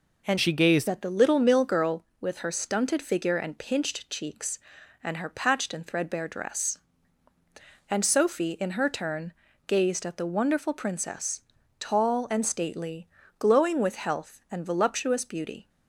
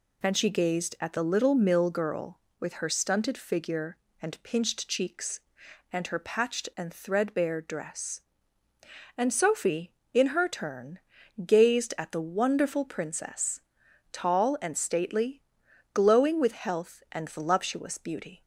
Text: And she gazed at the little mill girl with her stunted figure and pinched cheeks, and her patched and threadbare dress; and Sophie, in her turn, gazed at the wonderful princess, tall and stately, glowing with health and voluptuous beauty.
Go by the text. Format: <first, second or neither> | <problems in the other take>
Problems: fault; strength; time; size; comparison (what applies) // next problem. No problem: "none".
second | changes voice from "she" to "gazed"; from 0.3 to 0.8 s; 0.5 s long